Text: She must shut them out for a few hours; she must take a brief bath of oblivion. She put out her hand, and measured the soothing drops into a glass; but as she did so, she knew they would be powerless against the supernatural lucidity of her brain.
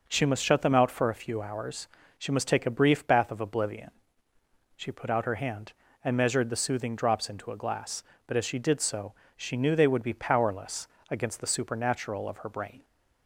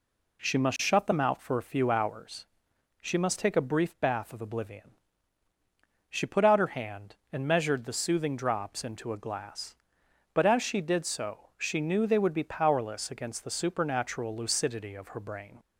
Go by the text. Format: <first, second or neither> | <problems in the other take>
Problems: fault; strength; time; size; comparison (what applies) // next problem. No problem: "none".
second | pauses between "powerless" and "against"; slight; at 10.8 s; 0.22 s long // skips "lucidity"; at 12.2 s